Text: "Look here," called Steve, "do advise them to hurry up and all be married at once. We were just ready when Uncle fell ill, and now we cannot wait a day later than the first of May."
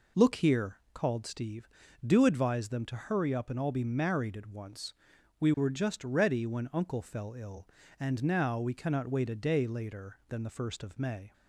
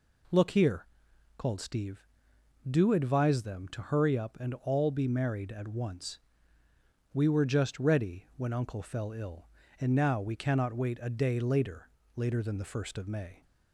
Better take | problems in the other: first | says "later" twice; at 12.1 s

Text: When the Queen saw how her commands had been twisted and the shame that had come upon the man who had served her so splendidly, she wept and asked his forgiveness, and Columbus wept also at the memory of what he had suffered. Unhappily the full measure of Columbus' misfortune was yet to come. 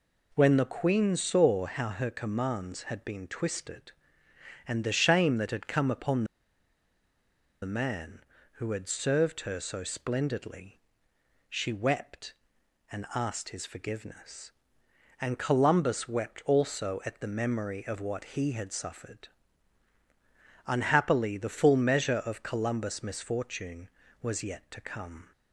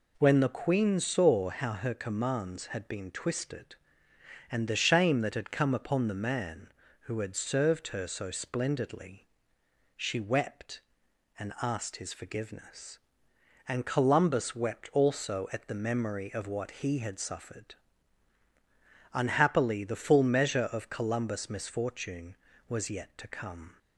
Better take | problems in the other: second | pauses between "upon" and "the"; strong; at 6.2 s; 1.3 s long

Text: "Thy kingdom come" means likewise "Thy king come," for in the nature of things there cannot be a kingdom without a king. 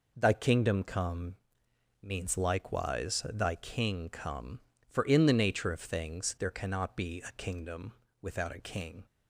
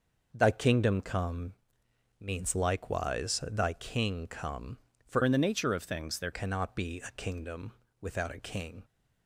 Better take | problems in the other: first | pauses between "come" and "means"; noticeable; at 1.5 s; 0.68 s long; noticeable in the first // changes voice from "in" to "there"; from 5.2 to 6.3 s; 1.1 s long // pauses between "kingdom" and "without"; slight; at 7.7 s; 0.26 s long; slight in the first

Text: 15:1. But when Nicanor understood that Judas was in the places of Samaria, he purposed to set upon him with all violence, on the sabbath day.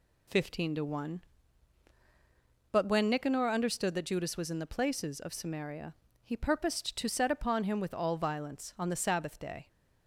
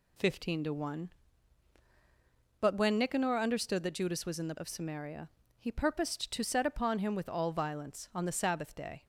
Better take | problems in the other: first | skips "places"; at 4.5 s

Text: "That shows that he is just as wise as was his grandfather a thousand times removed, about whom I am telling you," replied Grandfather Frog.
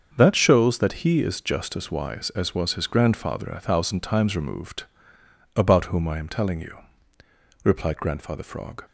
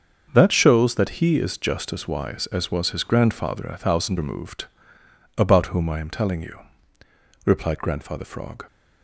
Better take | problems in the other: first | starts louder than the rest; until 1.3 s; 7 dB; also in the first // skips "times"; at 4.1 s

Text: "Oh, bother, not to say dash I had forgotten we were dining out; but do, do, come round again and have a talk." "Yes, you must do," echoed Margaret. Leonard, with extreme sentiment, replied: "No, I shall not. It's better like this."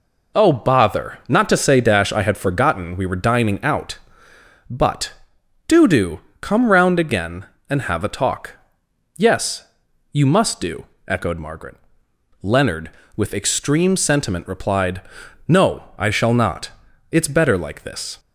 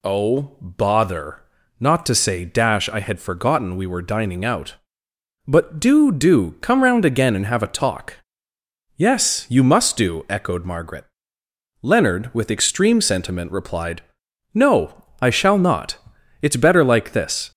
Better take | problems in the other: neither | none

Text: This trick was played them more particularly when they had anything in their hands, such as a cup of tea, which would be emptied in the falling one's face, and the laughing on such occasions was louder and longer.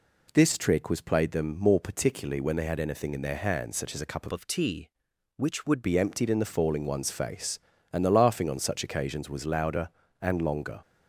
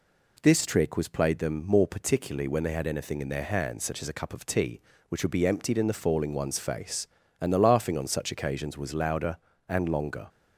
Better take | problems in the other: second | changes voice from "of" to "would"; from 4.3 to 5.8 s; 1.5 s long

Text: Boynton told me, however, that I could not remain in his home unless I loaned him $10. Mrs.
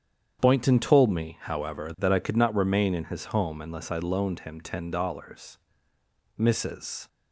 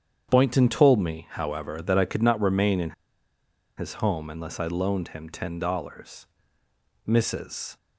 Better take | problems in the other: first | starts louder than the rest; strong; until 1.3 s; 8.5 dB; strong in the first // pauses between "in" and "his"; noticeable; at 2.9 s; 0.85 s long

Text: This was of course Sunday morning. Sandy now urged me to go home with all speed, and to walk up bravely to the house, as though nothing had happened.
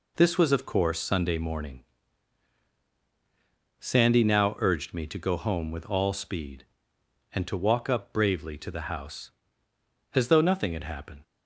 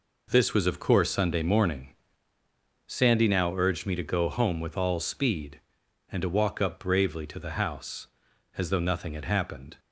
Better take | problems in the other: neither | none

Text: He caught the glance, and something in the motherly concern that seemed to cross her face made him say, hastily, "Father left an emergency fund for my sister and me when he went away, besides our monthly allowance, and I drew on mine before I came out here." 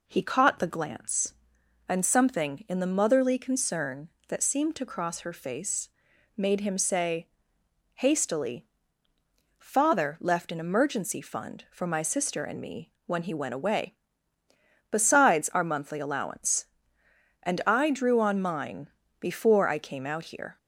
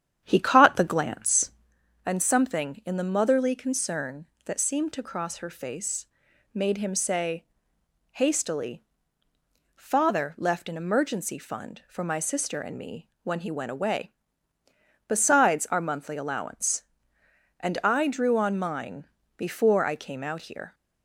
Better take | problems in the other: first | starts louder than the rest; strong; until 1.7 s; 9 dB // pauses between "face" and "made"; noticeable; at 6.0 s; 0.48 s long; noticeable in the first // pauses between "mine" and "before"; slight; at 19.0 s; 0.30 s long; slight in the first

